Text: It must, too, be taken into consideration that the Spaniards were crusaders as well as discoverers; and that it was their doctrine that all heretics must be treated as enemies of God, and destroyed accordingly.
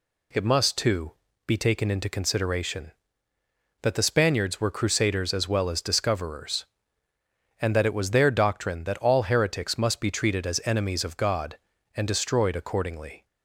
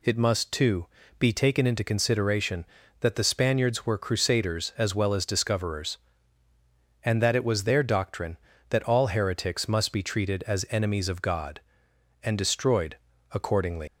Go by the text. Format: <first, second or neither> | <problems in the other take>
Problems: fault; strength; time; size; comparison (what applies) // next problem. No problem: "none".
first | pauses between "destroyed" and "accordingly"; slight; at 12.9 s; 0.34 s long // leaves "accordingly" unfinished; at 13.8 s; 115 ms